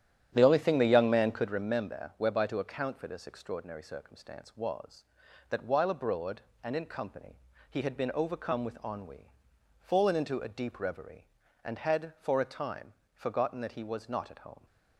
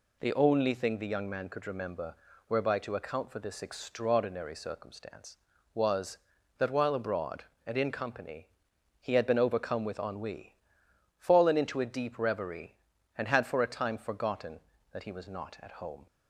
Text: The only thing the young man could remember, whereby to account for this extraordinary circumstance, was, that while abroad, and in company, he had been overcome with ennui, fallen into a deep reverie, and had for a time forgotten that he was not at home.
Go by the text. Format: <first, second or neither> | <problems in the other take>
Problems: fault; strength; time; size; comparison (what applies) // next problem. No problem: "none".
second | starts louder than the rest; strong; until 1.7 s; 10.5 dB // pauses between "time" and "forgotten"; slight; at 12.9 s; 0.20 s long